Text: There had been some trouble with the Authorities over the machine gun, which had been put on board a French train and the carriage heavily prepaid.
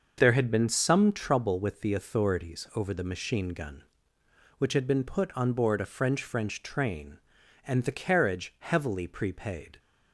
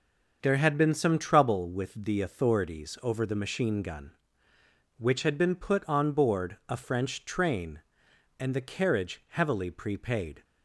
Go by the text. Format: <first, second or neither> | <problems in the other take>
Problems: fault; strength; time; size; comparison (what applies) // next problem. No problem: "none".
second | starts louder than the rest; noticeable; until 1.1 s; 6 dB; also in the second // says "French" twice; at 6.2 s